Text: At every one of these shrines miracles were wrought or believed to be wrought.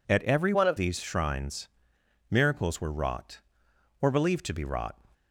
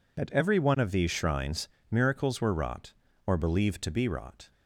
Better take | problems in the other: second | changes voice from "one" to "of"; from 0.5 to 0.7 s; 0.2 s long // pauses between "shrines" and "miracles"; noticeable; at 1.6 s; 0.62 s long; slight in the second

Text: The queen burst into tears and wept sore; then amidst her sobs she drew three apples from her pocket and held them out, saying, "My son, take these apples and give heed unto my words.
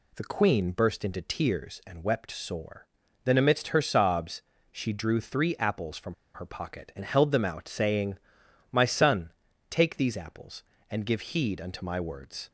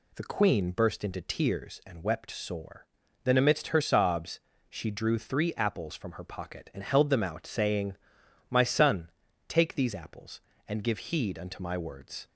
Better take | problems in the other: second | pauses between "sobs" and "she"; slight; at 4.4 s; 0.28 s long; slight in the second // pauses between "from" and "her"; slight; at 6.1 s; 0.20 s long

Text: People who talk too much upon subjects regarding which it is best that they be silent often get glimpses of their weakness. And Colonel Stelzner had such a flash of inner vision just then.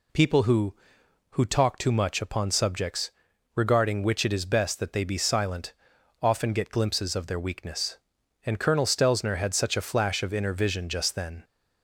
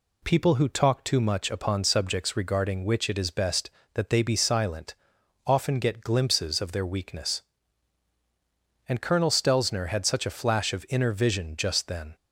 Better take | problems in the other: second | says "who" twice; at 1.3 s // pauses between "subjects" and "regarding"; at 3.1 s; 0.42 s long // pauses between "silent" and "often"; noticeable; at 5.7 s; 0.48 s long; noticeable in the second

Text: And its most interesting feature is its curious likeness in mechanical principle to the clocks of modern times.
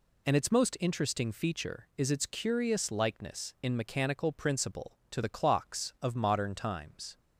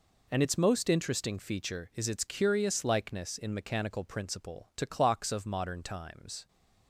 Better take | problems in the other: first | skips "the"; at 4.8 s

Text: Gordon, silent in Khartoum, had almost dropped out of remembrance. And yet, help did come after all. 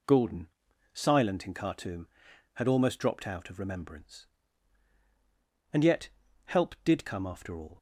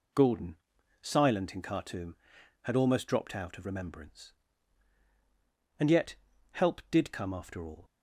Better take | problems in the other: neither | none

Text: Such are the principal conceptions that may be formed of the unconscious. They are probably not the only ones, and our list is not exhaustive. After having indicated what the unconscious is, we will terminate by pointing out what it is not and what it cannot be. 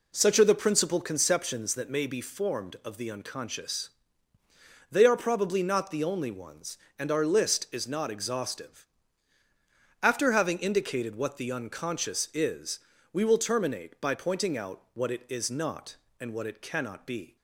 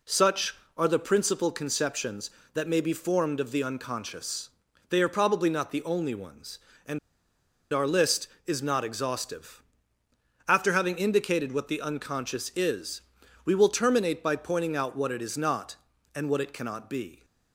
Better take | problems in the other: first | pauses between "and" and "our"; noticeable; at 6.9 s; 0.73 s long

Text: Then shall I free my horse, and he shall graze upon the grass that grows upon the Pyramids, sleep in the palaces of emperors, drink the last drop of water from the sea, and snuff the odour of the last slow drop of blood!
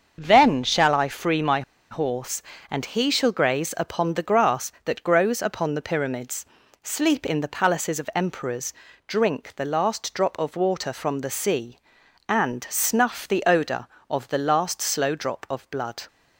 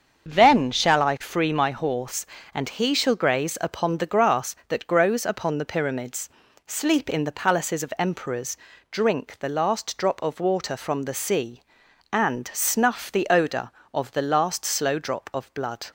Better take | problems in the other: second | starts louder than the rest; until 1.2 s; 7 dB; also in the second // pauses between "my" and "horse"; slight; at 1.6 s; 0.29 s long

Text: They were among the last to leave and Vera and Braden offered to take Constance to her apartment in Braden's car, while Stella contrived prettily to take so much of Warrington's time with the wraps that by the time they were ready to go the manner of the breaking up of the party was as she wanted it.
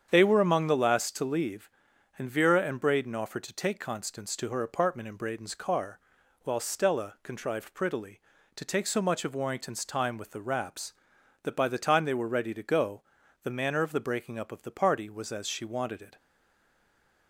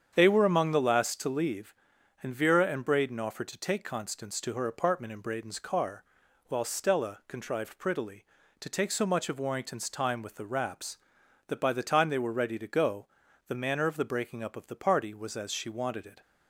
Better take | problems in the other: second | starts louder than the rest; strong; until 1.1 s; 8 dB; strong in the second // pauses between "go" and "the"; at 13.0 s; 0.40 s long; also in the second // stays silent after the last word; from 16.1 s on; 1.1 s long

